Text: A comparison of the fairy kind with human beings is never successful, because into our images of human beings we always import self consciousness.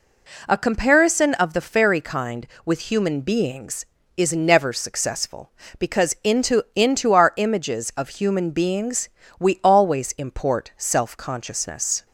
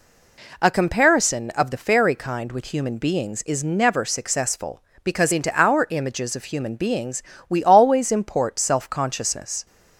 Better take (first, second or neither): second